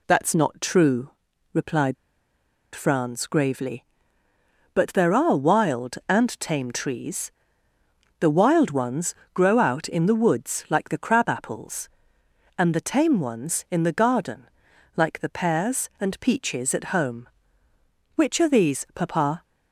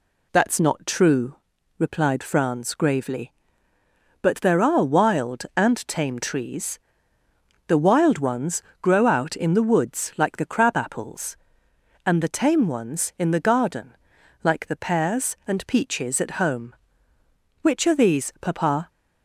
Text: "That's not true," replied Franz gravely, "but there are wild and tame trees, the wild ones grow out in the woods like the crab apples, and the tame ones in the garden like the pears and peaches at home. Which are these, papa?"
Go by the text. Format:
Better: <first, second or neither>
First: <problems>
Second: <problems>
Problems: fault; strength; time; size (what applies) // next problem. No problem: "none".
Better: second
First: pauses between "replied" and "Franz"; noticeable; at 1.9 s; 0.80 s long // pauses between "ones" and "grow"; slight; at 9.1 s; 0.22 s long // pauses between "garden" and "like"; noticeable; at 14.4 s; 0.48 s long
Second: pauses between "ones" and "grow"; slight; at 8.6 s; 0.22 s long // pauses between "garden" and "like"; noticeable; at 13.9 s; 0.48 s long